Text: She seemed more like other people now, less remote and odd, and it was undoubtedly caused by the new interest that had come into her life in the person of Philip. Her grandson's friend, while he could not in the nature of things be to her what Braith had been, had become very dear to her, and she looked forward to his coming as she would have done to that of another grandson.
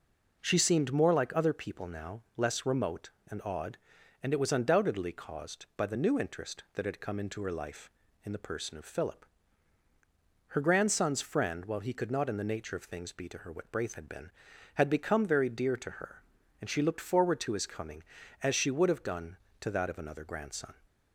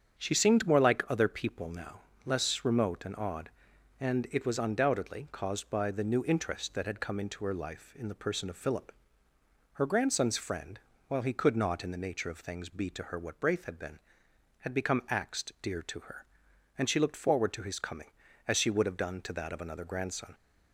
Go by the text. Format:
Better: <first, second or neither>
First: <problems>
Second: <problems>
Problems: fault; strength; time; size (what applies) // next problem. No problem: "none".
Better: first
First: none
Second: starts louder than the rest; strong; until 1.2 s; 8 dB // says "axed" for "very"; at 15.0 s